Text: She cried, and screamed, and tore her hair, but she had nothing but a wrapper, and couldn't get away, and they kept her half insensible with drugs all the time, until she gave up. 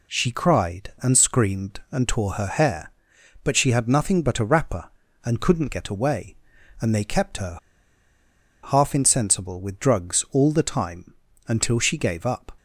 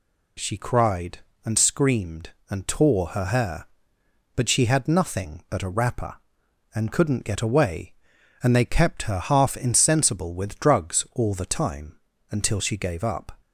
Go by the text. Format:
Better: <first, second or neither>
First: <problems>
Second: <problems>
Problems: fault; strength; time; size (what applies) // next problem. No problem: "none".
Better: second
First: pauses between "her" and "half"; at 7.5 s; 1.0 s long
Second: none